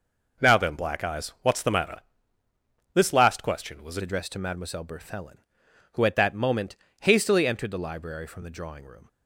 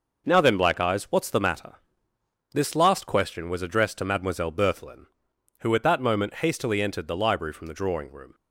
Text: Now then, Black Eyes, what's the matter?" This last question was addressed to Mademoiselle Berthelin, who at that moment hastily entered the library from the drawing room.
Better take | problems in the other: second | changes voice at "addressed"; from 4.0 s on; 5.0 s long // pauses between "moment" and "hastily"; slight; at 6.7 s; 0.26 s long

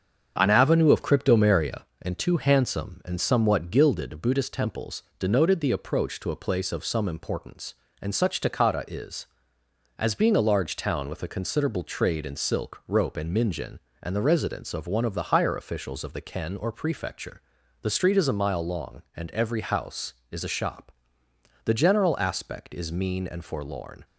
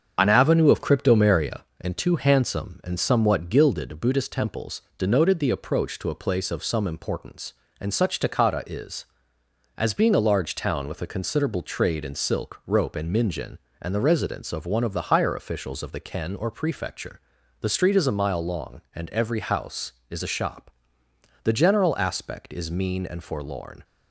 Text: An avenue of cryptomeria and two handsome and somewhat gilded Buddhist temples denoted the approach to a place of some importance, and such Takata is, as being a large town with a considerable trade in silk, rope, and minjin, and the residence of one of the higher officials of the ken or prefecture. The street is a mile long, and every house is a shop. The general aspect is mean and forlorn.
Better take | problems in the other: first | loses the start of "An"; at 0.1 s; 35 ms // starts louder than the rest; strong; until 1.1 s; 7 dB; strong in the first // pauses between "temples" and "denoted"; slight; at 4.7 s; 0.16 s long; slight in the first

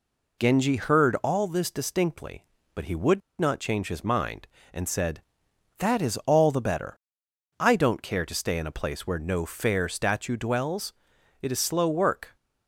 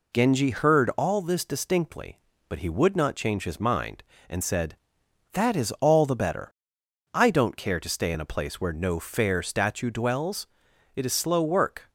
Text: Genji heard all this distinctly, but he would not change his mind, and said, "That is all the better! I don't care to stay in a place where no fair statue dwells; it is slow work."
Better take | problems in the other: second | pauses between "would" and "not"; slight; at 3.2 s; 0.19 s long

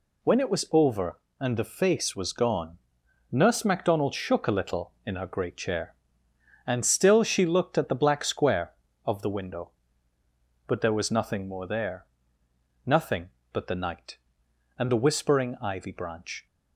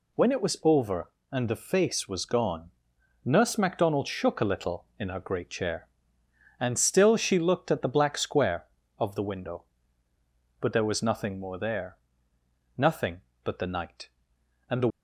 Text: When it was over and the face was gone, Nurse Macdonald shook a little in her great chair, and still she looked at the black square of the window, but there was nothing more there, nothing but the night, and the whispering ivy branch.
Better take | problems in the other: first | stops before "whispering ivy branch"; at 14.9 s

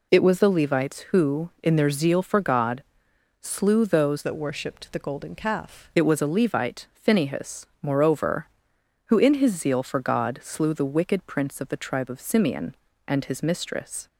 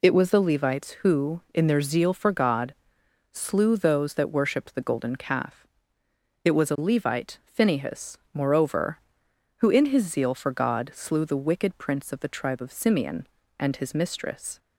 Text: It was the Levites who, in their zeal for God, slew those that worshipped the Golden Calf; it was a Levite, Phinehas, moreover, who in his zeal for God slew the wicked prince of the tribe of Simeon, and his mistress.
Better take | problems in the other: second | changes voice from "that" to "Calf"; from 4.2 to 5.8 s; 1.6 s long

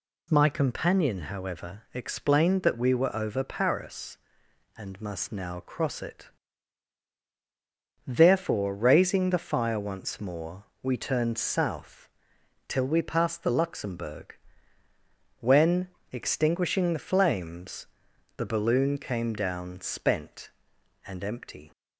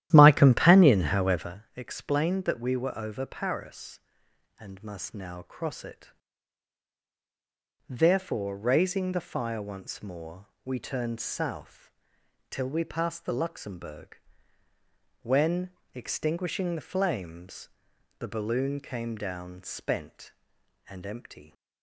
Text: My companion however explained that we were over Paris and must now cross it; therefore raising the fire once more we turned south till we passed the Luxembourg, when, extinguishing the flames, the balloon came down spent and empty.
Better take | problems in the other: first | starts louder than the rest; strong; until 1.6 s; 12.5 dB // pauses between "more" and "we"; slight; at 10.4 s; 0.18 s long; slight in the first // pauses between "south" and "till"; noticeable; at 11.9 s; 0.58 s long; noticeable in the first

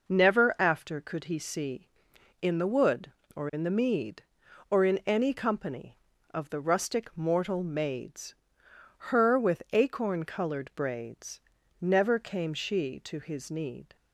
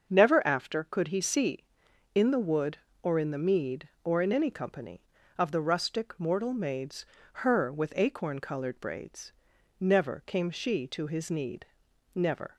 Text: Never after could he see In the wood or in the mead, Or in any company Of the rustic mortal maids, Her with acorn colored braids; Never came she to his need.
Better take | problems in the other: first | starts louder than the rest; until 1.1 s; 6.5 dB // goes on to say "Never"; slight; from 12.1 s on; 0.42 s long

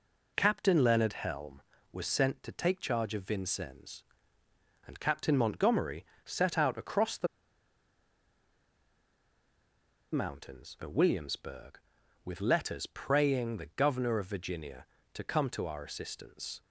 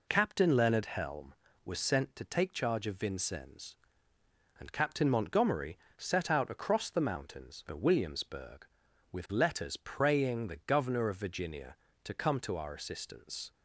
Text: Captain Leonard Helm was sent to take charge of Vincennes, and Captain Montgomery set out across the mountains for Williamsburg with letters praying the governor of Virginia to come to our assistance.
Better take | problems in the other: second | pauses between "Montgomery" and "set"; slight; at 6.0 s; 0.20 s long; slight in the second // pauses between "the" and "mountains"; strong; at 7.2 s; 2.8 s long

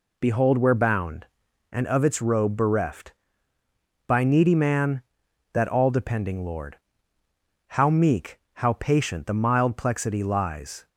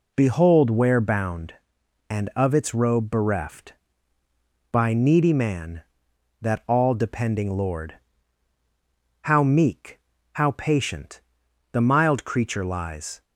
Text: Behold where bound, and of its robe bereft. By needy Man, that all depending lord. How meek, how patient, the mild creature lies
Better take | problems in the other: second | says "plexity" for "creature"; at 9.7 s

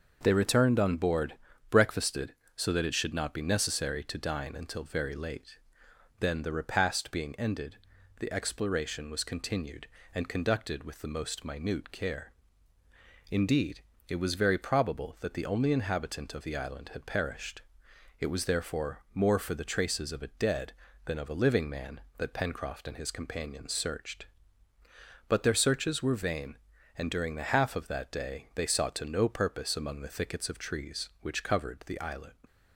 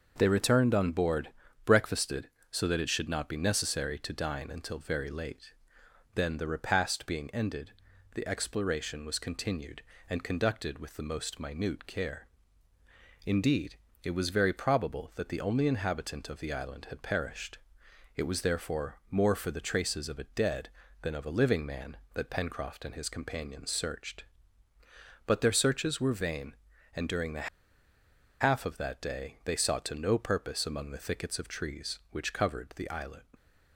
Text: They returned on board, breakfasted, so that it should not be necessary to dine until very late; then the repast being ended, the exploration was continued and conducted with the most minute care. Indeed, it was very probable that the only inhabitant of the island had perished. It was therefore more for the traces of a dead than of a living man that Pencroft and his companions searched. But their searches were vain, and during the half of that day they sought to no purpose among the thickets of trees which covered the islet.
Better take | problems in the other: first | starts louder than the rest; noticeable; until 1.1 s; 6 dB; noticeable in the first // pauses between "the" and "half"; noticeable; at 27.4 s; 0.93 s long

